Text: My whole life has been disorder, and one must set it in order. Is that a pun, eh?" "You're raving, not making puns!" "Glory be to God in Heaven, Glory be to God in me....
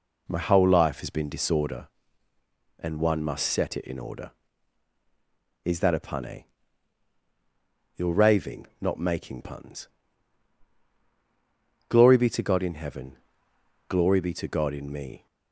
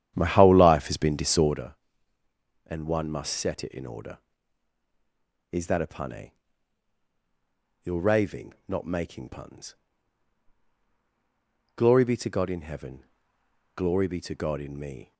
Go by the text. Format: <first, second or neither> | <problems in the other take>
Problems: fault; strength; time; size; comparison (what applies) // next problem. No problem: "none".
first | starts louder than the rest; strong; until 1.7 s; 10 dB